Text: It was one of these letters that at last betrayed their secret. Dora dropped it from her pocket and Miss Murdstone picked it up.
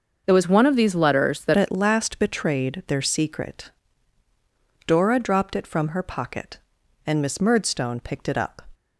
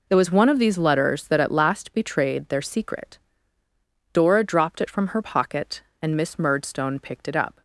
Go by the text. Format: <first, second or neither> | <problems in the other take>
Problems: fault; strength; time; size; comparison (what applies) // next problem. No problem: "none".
second | starts louder than the rest; until 1.2 s; 6 dB // changes voice at "at"; from 1.5 s on; 7.1 s long